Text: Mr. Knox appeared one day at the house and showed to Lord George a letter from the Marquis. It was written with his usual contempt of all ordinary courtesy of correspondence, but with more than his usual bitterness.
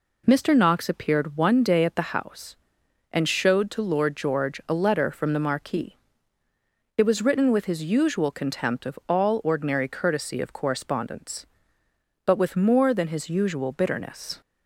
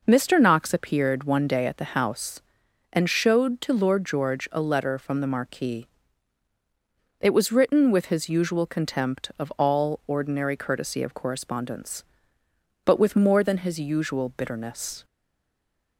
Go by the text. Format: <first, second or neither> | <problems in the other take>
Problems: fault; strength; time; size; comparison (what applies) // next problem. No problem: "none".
first | stays silent after the last word; slight; from 15.0 s on; 0.9 s long